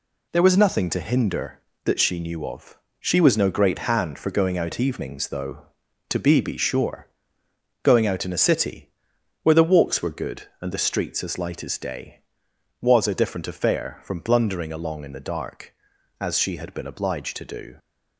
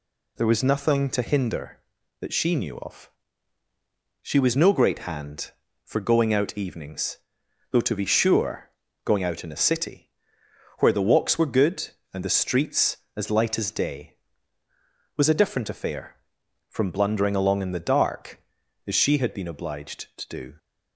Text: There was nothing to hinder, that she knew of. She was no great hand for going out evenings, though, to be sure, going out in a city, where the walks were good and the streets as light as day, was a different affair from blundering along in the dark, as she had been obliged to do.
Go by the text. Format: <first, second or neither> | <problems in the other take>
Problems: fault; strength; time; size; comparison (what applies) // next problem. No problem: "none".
second | says "be" twice; at 6.4 s